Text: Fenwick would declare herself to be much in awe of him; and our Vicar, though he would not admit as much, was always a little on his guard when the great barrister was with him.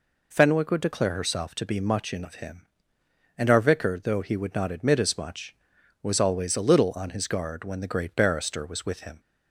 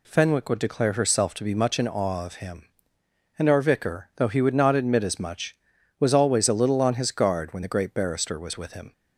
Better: second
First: skips "awe"; at 2.2 s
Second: none

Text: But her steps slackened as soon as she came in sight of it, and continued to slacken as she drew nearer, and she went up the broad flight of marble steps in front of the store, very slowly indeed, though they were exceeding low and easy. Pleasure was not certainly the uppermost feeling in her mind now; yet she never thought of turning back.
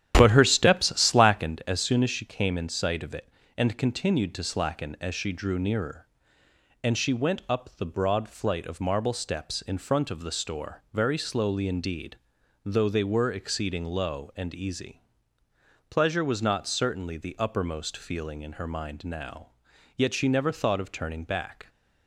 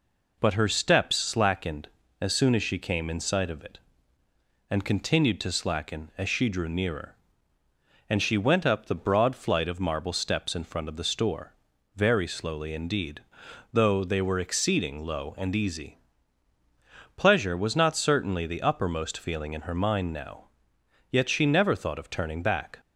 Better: second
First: starts louder than the rest; strong; until 1.6 s; 10.5 dB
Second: none

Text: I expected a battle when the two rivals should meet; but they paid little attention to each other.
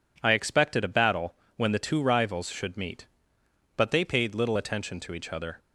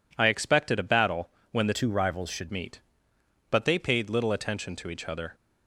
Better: first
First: pauses between "battle" and "when"; slight; at 1.3 s; 0.22 s long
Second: pauses between "battle" and "when"; slight; at 1.2 s; 0.22 s long // changes voice from "two" to "should"; from 1.7 to 2.4 s; 0.7 s long

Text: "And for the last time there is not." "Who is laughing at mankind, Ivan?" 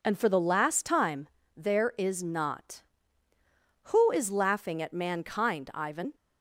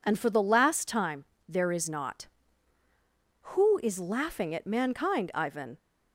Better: neither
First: pauses between "time" and "there"; slight; at 1.2 s; 0.26 s long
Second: pauses between "time" and "there"; slight; at 1.2 s; 0.24 s long

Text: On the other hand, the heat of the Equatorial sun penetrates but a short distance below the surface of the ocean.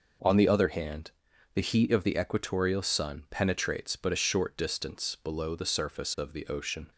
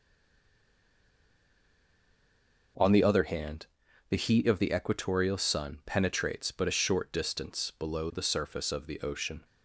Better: first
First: none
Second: stays silent before the first word; strong; until 2.7 s; 2.7 s long

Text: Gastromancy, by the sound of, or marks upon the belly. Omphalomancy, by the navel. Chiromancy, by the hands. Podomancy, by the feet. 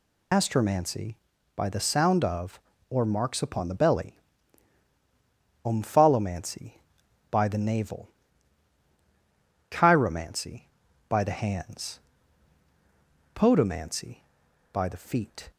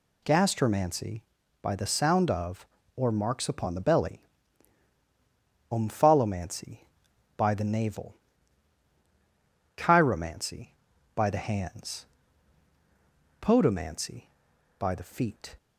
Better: second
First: loses the start of "Gastromancy"; at 0.3 s; 135 ms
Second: none

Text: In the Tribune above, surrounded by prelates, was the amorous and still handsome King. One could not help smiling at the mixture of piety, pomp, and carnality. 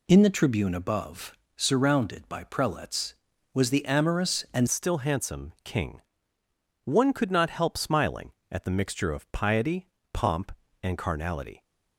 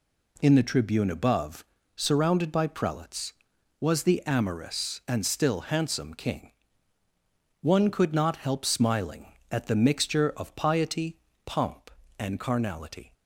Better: second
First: changes voice at "still"; from 4.6 s on; 7.0 s long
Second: none

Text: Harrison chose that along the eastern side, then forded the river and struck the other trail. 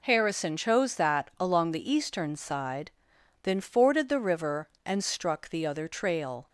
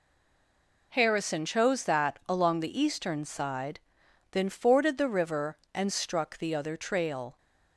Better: first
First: none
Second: stays silent before the first word; slight; until 0.9 s; 0.9 s long

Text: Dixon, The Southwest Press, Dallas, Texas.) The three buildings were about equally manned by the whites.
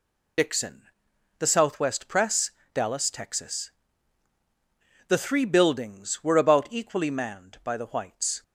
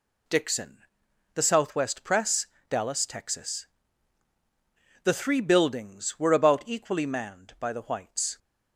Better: second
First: loses the start of "Dixon"; at 0.3 s; 55 ms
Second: none

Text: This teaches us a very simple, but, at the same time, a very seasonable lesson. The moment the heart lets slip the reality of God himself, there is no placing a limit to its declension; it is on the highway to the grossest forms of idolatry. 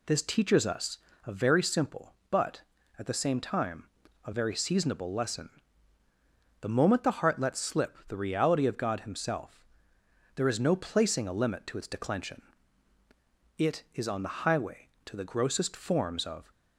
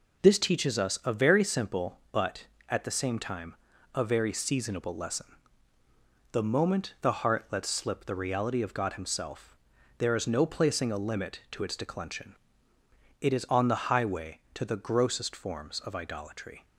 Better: second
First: pauses between "us" and "a"; slight; at 0.9 s; 0.26 s long // stops before "idolatry"; at 16.5 s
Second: none

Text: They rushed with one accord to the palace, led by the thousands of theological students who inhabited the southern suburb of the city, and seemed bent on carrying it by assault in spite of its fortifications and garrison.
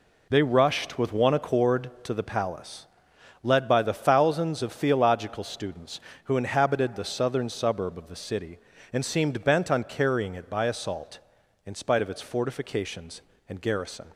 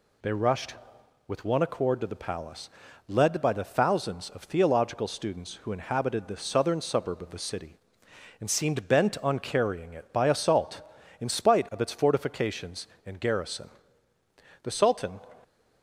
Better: first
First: none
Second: goes on to say "The Sultan"; from 14.6 s on; 0.58 s long

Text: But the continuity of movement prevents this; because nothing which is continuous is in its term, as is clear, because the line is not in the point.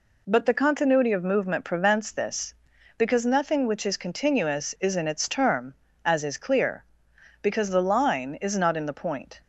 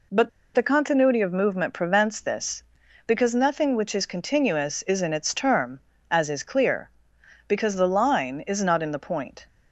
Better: first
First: none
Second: pauses between "But" and "the"; slight; at 0.2 s; 0.25 s long

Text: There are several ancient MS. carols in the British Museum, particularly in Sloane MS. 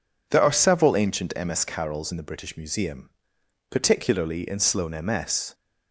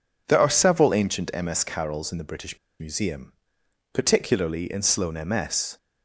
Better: first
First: none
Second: pauses between "British" and "Museum"; slight; at 2.5 s; 0.22 s long

